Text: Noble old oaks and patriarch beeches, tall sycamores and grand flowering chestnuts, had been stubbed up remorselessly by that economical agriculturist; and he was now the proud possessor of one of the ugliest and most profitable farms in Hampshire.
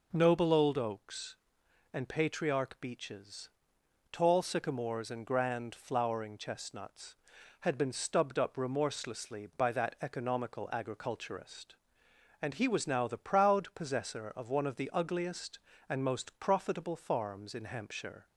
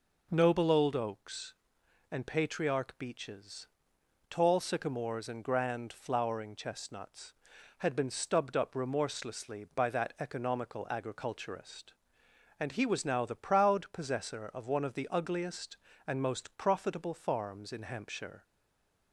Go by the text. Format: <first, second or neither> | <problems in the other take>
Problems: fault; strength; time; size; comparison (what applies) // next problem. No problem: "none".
first | stays silent after the last word; slight; from 18.4 s on; 0.7 s long